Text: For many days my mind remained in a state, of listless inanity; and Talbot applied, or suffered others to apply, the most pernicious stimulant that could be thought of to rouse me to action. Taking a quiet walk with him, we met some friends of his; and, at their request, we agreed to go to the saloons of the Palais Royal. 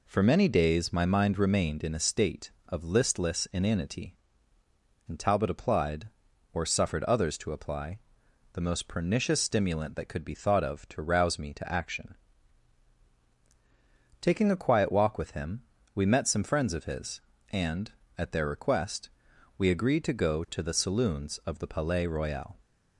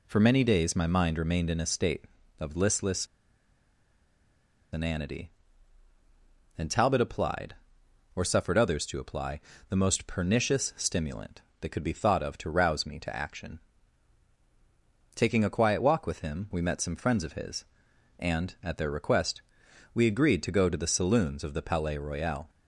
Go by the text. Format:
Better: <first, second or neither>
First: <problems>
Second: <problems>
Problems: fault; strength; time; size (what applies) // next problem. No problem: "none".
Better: first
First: none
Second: pauses between "listless" and "inanity"; strong; at 3.0 s; 1.6 s long